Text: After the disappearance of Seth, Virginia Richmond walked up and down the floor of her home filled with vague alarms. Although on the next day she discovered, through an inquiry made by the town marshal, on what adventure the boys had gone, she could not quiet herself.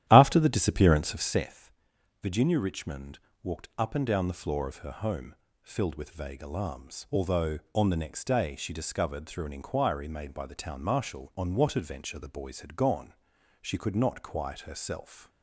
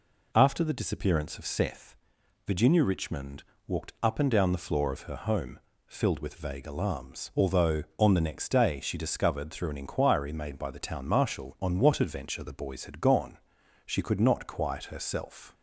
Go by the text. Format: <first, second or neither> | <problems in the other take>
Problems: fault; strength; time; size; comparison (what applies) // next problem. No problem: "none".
second | starts louder than the rest; strong; until 1.5 s; 12 dB // pauses between "Richmond" and "walked"; slight; at 3.1 s; 0.24 s long; slight in the second // pauses between "home" and "filled"; slight; at 5.3 s; 0.28 s long; slight in the second